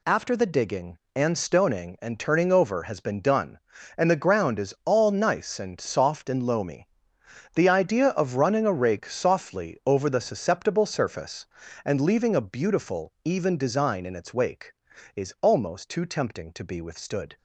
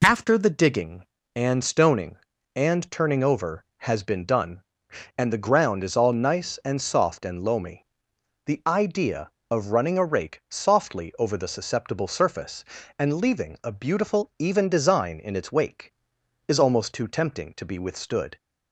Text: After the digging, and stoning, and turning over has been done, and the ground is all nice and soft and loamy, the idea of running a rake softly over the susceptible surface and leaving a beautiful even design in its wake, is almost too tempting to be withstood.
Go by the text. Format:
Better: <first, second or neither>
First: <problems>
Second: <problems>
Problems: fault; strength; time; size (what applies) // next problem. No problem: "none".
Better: neither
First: none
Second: none